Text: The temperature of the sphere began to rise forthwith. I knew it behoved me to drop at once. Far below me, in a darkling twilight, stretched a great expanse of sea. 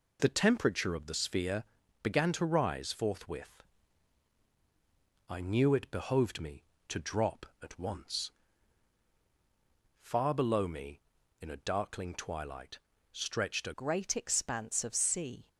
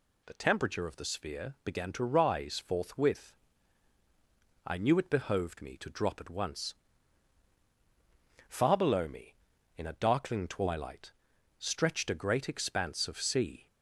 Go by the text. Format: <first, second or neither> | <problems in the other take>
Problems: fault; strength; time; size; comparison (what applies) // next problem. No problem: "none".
second | pauses between "sphere" and "began"; at 1.6 s; 0.40 s long // changes voice at "great"; from 13.7 s on; 1.7 s long